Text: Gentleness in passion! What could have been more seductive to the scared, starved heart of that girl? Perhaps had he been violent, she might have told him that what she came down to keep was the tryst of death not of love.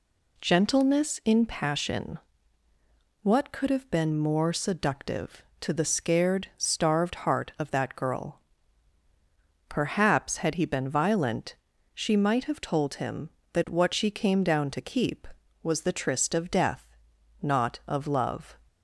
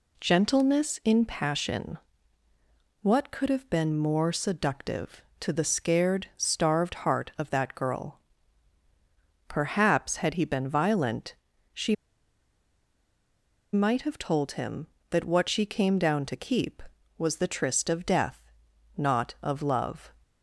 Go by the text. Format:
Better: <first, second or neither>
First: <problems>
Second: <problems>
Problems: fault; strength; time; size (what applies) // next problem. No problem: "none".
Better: first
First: pauses between "death" and "not"; noticeable; at 16.8 s; 0.56 s long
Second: pauses between "she" and "might"; strong; at 11.9 s; 1.7 s long // pauses between "death" and "not"; noticeable; at 18.4 s; 0.56 s long